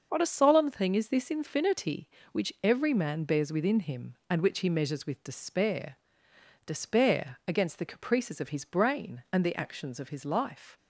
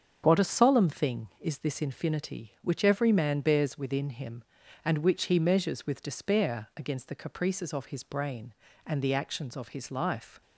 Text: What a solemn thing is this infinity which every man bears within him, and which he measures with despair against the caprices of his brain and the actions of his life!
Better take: second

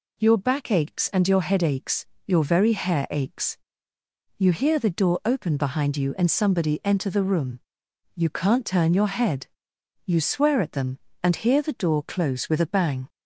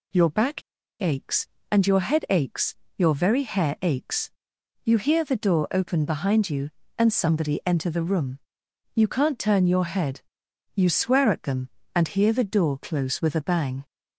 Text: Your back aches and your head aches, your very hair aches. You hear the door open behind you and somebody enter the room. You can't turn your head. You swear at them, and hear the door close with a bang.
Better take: first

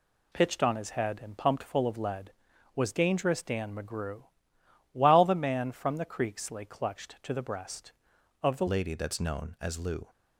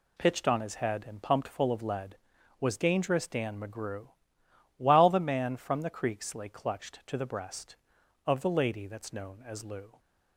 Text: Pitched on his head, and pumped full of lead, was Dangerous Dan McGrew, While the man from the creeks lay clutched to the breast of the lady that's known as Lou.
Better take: second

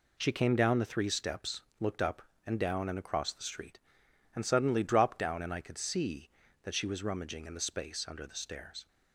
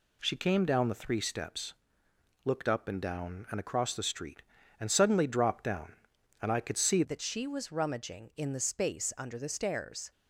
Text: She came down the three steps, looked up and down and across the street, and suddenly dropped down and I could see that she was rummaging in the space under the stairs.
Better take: first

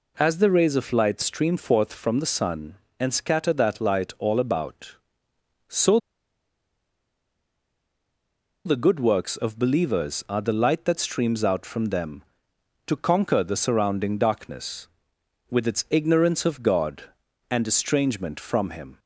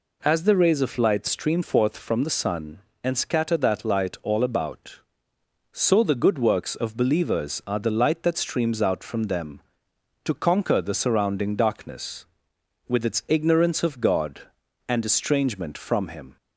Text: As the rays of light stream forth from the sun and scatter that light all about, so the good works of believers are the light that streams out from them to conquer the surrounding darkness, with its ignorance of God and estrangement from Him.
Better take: second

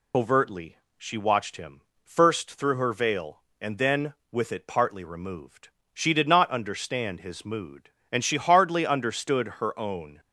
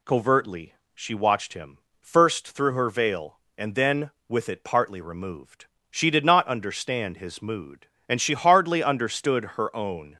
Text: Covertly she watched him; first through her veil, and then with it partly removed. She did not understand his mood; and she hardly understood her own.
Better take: second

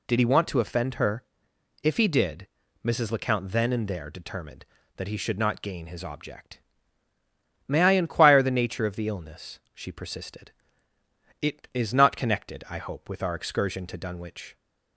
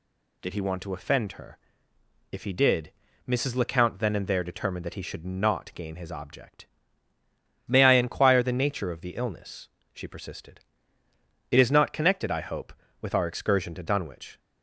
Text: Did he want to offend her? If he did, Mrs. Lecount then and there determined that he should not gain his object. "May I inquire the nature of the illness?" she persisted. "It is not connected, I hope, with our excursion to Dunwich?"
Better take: neither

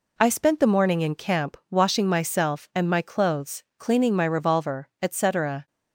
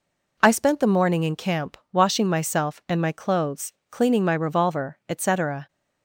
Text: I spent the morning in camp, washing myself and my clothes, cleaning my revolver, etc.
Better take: neither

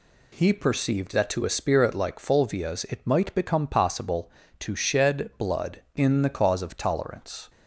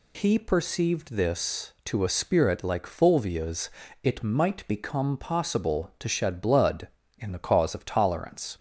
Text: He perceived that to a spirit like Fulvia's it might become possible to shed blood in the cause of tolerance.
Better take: first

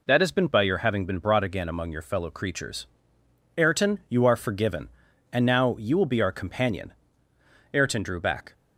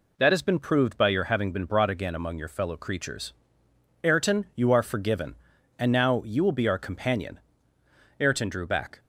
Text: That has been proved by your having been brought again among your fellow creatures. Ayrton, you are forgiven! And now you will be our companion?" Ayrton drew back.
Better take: second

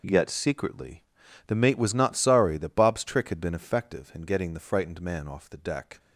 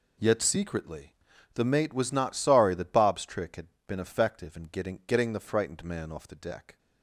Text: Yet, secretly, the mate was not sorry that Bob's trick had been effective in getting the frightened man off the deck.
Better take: first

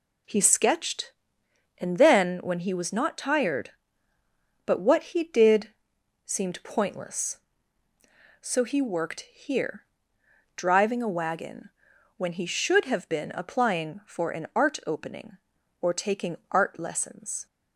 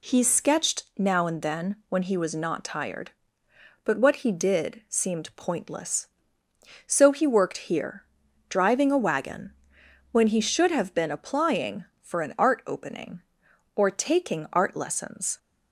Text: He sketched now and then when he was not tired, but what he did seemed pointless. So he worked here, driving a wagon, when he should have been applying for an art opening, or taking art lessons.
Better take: second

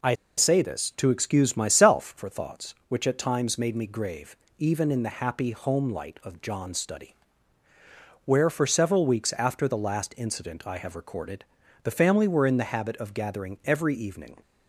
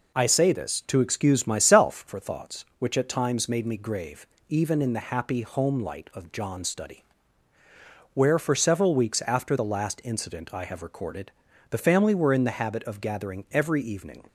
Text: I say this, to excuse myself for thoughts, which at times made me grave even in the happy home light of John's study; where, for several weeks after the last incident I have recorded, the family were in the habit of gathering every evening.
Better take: second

